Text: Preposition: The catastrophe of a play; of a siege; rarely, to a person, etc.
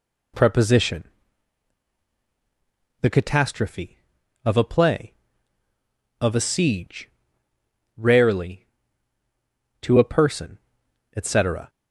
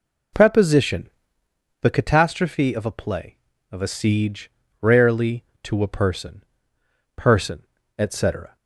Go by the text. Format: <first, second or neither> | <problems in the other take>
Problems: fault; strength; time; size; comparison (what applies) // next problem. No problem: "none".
first | says "person" twice; at 7.1 s